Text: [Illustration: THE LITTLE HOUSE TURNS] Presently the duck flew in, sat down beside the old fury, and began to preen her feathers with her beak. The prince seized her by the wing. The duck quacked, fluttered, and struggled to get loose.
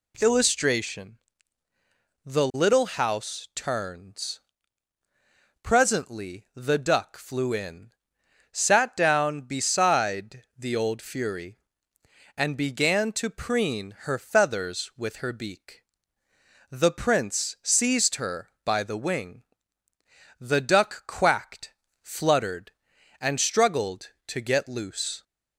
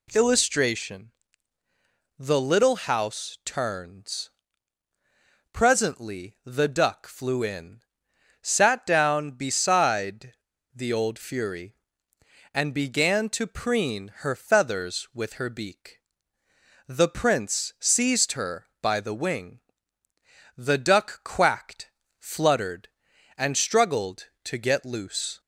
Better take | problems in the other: first | pauses between "TURNS" and "Presently"; at 4.3 s; 1.2 s long; also in the first // pauses between "beside" and "the"; at 10.3 s; 0.41 s long

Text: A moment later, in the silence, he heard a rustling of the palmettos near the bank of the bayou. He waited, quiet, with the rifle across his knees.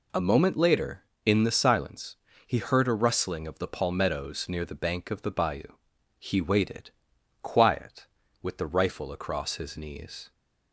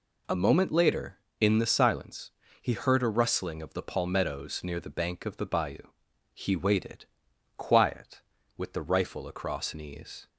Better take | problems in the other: first | skips "his"; at 9.7 s

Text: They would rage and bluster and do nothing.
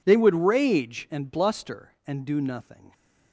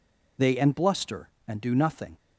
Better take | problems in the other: first | skips "would rage"; at 0.5 s

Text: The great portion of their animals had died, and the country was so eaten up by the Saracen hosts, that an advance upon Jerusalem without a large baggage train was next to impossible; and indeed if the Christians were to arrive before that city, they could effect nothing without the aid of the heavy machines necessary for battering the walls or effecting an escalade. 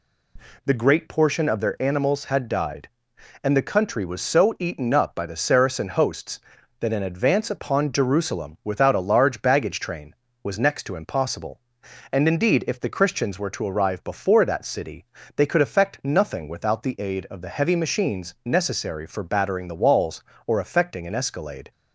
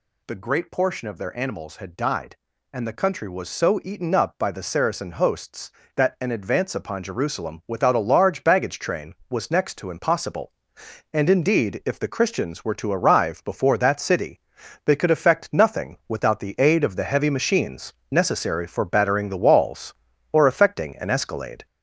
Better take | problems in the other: first | gets louder; noticeable; throughout; 5 dB // pauses between "machines" and "necessary"; slight; at 17.9 s; 0.18 s long

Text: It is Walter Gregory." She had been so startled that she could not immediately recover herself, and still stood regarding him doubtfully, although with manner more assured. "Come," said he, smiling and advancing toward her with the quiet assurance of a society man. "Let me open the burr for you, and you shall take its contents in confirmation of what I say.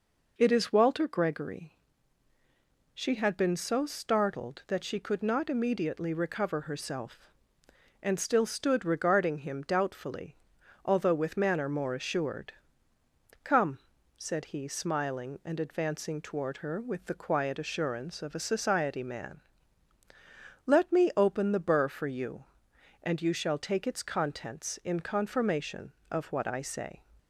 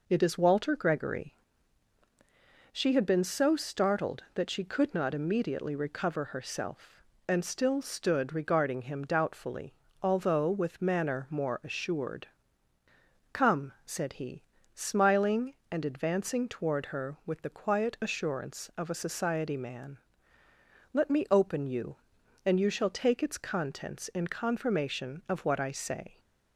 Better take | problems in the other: first | skips "the burr for"; at 21.6 s

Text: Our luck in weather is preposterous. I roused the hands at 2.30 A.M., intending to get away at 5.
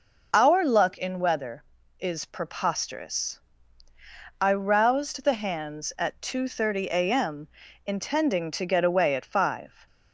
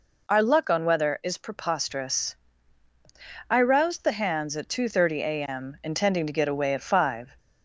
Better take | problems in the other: first | says "on" for "in"; at 0.6 s

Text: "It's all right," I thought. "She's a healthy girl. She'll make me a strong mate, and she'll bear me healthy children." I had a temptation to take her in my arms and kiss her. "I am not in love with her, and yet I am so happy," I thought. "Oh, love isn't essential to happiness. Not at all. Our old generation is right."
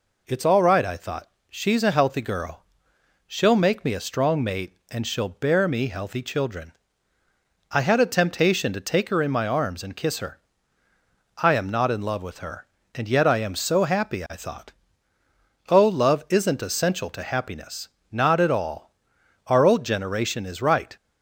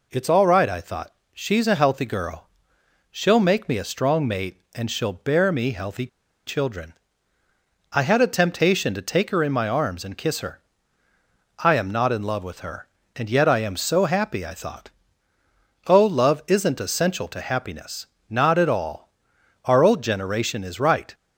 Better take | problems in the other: first | pauses between "healthy" and "children"; at 6.0 s; 0.39 s long

